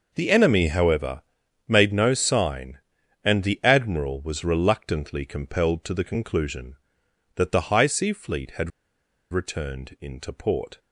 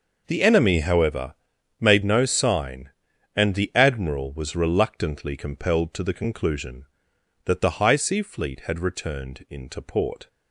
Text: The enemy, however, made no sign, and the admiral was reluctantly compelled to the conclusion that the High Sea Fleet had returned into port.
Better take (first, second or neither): second